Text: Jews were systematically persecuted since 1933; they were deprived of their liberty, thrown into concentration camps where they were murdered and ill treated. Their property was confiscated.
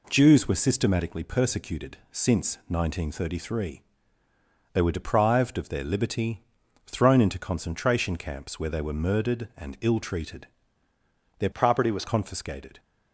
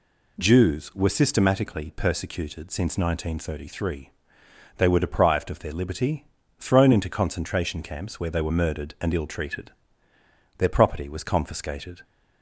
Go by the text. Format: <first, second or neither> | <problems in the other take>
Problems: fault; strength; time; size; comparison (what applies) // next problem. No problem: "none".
second | changes voice from "property" to "was"; from 11.5 to 12.0 s; 0.5 s long